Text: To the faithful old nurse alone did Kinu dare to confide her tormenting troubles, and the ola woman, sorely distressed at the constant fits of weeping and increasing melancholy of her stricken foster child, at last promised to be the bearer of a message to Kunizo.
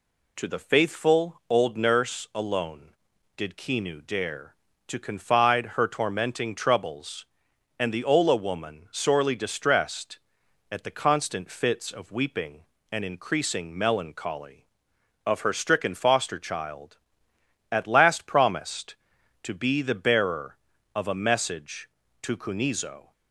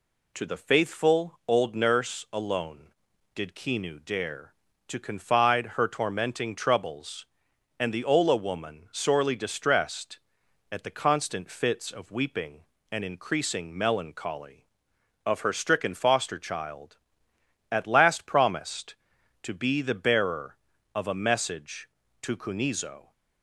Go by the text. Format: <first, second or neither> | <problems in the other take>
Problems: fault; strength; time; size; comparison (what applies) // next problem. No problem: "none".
neither | none